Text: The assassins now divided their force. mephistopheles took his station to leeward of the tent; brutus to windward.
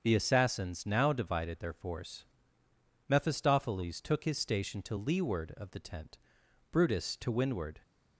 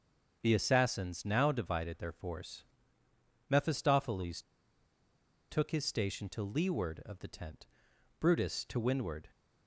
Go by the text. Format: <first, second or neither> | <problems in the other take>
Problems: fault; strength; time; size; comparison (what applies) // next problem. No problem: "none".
first | starts louder than the rest; until 1.4 s; 7 dB; also in the first // pauses between "mephistopheles" and "took"; at 4.4 s; 1.0 s long